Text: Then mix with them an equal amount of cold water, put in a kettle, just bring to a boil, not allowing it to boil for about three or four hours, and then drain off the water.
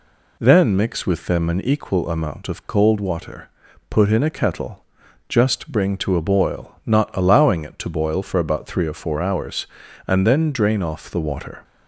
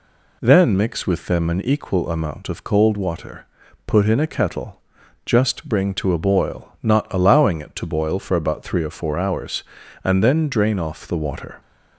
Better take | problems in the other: neither | none

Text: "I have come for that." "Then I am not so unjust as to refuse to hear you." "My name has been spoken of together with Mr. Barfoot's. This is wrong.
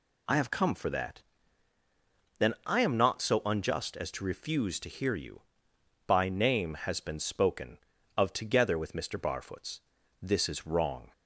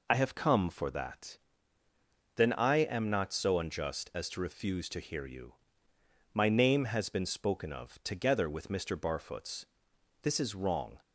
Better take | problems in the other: second | says "By" for "My"; at 6.0 s

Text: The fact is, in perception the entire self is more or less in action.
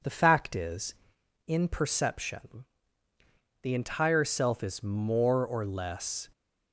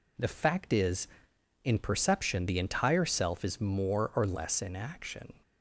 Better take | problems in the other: second | pauses between "perception" and "the"; noticeable; at 2.6 s; 0.98 s long // stops before "in action"; at 6.3 s

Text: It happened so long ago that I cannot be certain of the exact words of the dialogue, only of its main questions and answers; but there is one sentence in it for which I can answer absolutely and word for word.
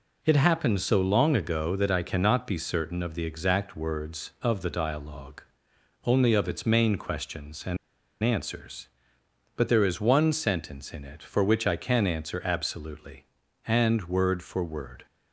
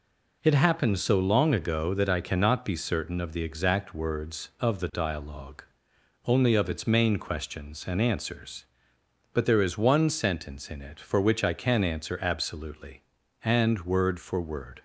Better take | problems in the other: second | pauses between "and" and "answers"; noticeable; at 7.7 s; 0.46 s long

